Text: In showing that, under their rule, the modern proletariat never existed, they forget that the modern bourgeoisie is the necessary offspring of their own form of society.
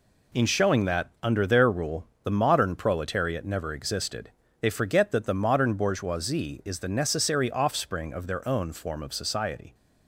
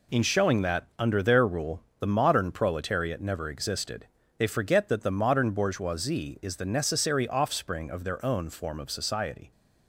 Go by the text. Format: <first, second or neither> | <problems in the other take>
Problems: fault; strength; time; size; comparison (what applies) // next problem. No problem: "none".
neither | none